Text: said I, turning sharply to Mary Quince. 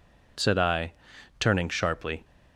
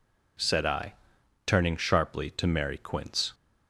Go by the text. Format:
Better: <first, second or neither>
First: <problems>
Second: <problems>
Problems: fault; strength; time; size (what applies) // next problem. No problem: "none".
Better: second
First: stops before "to Mary Quince"; at 2.2 s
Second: none